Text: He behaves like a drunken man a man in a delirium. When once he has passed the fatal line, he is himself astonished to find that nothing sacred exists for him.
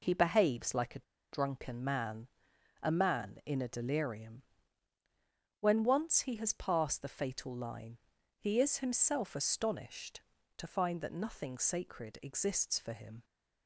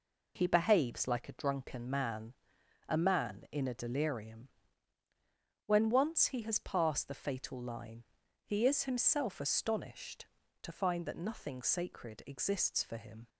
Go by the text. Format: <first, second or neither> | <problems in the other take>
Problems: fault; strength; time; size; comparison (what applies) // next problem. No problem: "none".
second | pauses between "a" and "drunken"; slight; at 1.0 s; 0.27 s long // pauses between "man" and "a"; noticeable; at 2.2 s; 0.52 s long; noticeable in the second